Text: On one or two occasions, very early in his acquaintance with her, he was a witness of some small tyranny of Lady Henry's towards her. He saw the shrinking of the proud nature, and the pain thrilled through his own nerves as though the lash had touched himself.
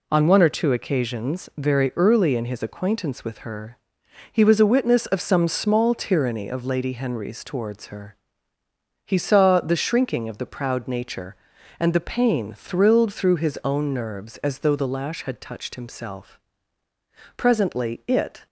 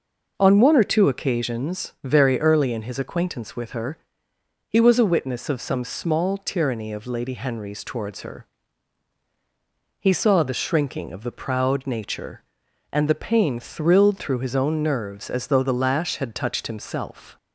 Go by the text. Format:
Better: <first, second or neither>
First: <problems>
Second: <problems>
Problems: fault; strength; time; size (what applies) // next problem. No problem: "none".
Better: second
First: goes on to say "Presently it"; noticeable; from 17.3 s on; 1.1 s long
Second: none